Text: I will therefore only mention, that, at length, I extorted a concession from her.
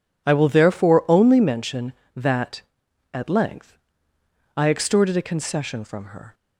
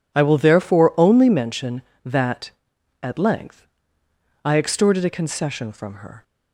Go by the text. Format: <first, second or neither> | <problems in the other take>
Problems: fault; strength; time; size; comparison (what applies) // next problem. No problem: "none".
neither | none